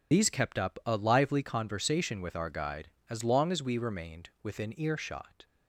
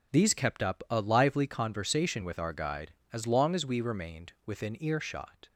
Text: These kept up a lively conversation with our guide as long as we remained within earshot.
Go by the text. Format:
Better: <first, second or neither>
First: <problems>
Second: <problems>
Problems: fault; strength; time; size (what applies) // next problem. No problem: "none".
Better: second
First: loses the start of "These"; at 0.1 s; 45 ms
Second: none